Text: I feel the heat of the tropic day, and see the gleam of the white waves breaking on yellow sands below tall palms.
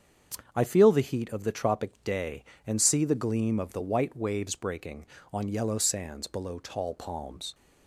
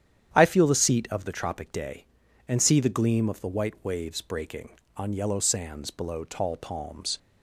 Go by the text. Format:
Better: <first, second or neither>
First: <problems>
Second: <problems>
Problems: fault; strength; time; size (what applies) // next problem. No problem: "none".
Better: first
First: starts louder than the rest; strong; until 1.5 s; 7.5 dB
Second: starts louder than the rest; strong; until 1.3 s; 9.5 dB // says "seat" for "heat"; at 0.7 s